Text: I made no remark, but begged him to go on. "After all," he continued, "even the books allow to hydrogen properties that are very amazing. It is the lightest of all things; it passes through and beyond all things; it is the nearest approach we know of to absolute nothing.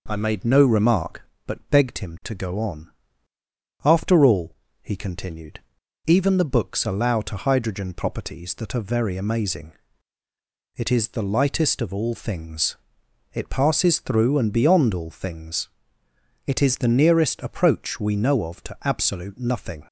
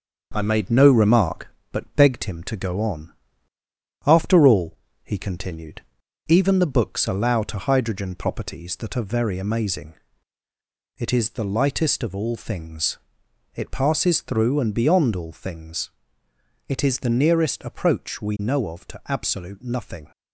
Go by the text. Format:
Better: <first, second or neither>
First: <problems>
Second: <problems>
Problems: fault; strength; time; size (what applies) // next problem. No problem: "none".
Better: first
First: none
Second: gets quieter; throughout; 3.5 dB